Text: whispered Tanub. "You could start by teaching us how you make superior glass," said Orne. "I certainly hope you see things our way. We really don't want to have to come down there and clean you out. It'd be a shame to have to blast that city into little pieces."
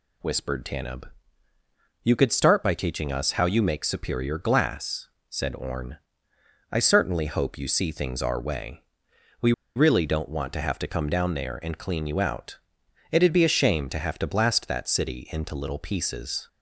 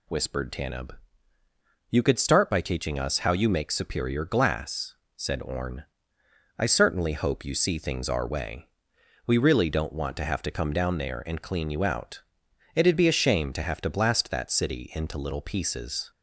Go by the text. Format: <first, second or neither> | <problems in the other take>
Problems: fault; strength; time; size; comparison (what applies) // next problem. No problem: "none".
second | pauses between "We" and "really"; slight; at 9.5 s; 0.23 s long